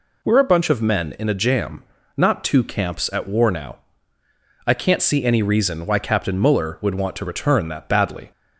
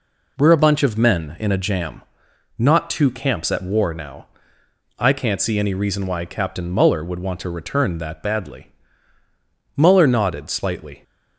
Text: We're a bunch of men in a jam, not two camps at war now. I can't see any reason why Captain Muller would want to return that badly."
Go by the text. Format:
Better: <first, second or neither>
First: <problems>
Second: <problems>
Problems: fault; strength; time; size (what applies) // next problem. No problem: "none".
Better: first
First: none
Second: goes on to say "Muller nodded slightly"; noticeable; from 9.7 s on; 1.2 s long